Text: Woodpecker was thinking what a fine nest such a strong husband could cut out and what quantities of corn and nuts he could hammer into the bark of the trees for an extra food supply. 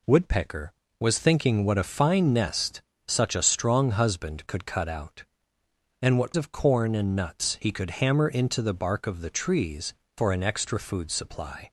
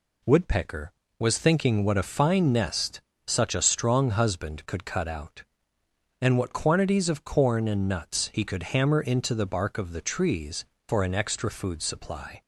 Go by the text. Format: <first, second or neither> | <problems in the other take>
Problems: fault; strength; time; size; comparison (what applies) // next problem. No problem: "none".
second | pauses between "nest" and "such"; slight; at 2.8 s; 0.26 s long; slight in the second // skips "quantities"; at 6.3 s